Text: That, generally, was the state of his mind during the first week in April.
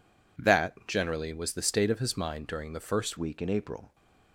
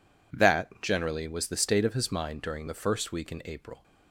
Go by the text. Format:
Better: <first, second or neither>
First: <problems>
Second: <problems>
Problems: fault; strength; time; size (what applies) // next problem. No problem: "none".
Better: second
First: changes voice at "week"; from 3.1 s on; 0.8 s long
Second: none